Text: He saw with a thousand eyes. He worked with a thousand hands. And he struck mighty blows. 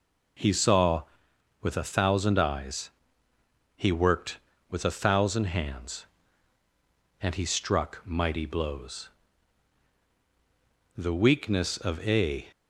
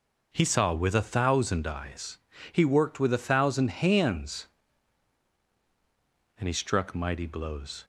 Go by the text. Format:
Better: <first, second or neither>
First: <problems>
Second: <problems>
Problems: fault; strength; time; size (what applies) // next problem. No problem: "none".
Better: second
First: goes on to say "The weakness of a"; from 10.9 s on; 1.5 s long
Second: none